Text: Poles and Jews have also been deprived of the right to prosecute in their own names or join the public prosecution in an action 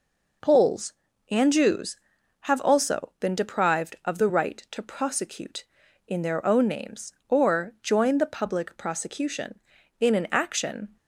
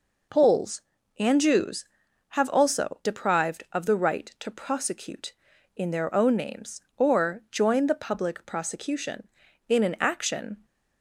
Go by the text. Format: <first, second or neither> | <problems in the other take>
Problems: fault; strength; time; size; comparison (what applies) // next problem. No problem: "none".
first | skips "been"; at 3.0 s